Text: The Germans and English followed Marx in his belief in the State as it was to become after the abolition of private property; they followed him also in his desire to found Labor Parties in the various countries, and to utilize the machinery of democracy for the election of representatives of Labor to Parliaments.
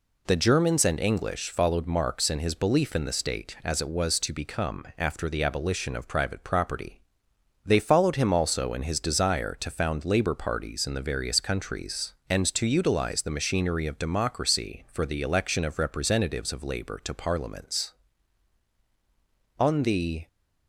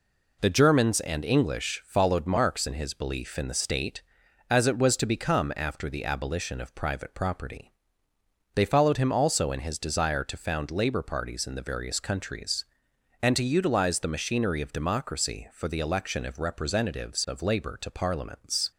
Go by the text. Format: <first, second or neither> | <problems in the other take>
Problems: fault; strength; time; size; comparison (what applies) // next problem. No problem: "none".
second | goes on to say "On the"; noticeable; from 19.5 s on; 0.68 s long